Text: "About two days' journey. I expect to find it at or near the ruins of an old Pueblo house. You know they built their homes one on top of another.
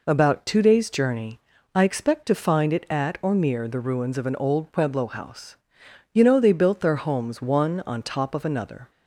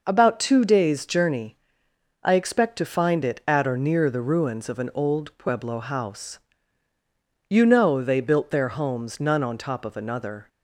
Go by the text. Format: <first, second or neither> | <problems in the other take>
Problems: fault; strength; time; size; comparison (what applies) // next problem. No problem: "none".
first | says "none" for "one"; at 9.1 s